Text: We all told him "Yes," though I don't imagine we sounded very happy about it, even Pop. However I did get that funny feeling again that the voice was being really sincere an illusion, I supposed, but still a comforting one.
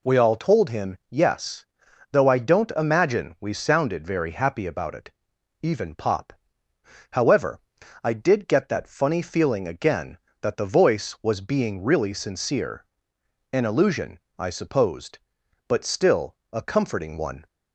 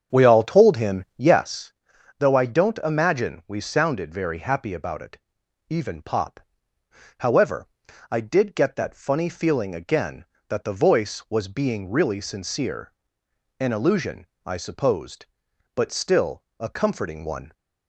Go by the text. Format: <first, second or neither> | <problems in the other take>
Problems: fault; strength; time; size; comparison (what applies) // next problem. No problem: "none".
first | starts louder than the rest; strong; until 1.6 s; 7.5 dB // pauses between "However" and "I"; at 7.6 s; 0.44 s long; also in the first // pauses between "sincere" and "an"; noticeable; at 12.9 s; 0.66 s long; noticeable in the first // pauses between "still" and "a"; slight; at 16.4 s; 0.16 s long; slight in the first